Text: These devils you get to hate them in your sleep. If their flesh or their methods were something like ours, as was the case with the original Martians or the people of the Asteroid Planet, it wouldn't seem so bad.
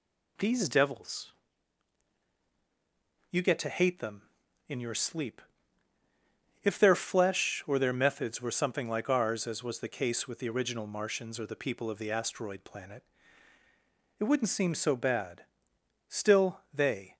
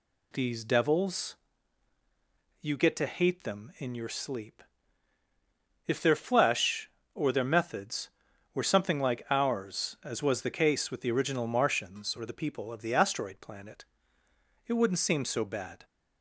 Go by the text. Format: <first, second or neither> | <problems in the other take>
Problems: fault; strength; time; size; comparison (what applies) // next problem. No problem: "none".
second | pauses between "devils" and "you"; strong; at 1.3 s; 2.0 s long; strong in the second // goes on to say "Still they"; noticeable; from 16.0 s on; 1.0 s long